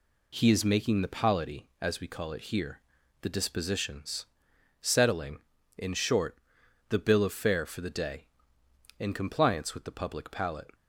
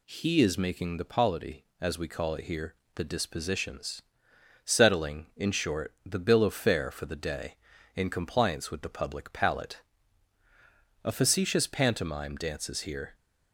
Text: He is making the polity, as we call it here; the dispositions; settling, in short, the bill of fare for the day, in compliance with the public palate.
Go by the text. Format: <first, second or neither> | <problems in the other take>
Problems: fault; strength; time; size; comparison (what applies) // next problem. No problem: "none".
first | goes on to say "A facetious pantomime dances here"; strong; from 11.0 s on; 2.1 s long